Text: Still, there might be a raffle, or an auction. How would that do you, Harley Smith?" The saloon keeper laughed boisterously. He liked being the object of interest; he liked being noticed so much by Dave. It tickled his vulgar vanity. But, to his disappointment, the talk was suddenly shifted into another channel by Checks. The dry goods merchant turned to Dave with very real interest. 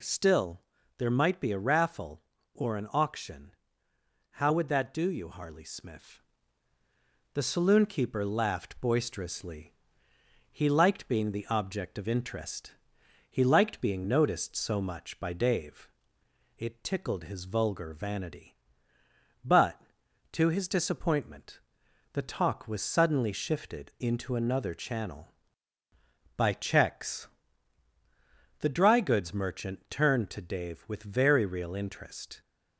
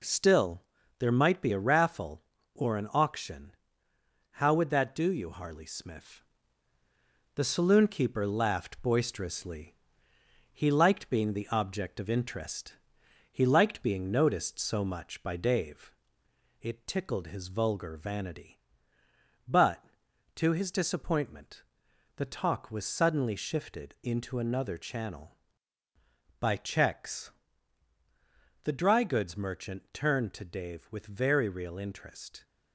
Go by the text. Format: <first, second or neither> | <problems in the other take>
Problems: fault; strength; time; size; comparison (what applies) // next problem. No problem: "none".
first | gets quieter; noticeable; throughout; 4.5 dB